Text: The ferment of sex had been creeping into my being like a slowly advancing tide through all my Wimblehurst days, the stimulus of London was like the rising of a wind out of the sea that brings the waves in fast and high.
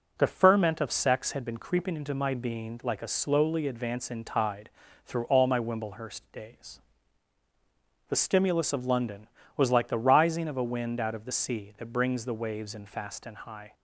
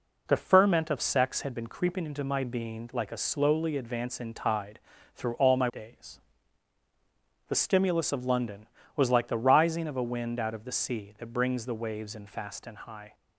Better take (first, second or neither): first